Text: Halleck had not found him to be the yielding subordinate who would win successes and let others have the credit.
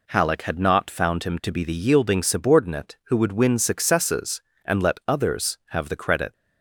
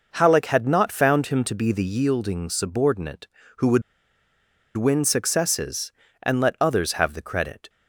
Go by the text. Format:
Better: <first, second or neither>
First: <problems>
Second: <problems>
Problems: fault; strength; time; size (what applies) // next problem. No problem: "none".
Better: first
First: none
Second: pauses between "would" and "win"; noticeable; at 3.8 s; 0.95 s long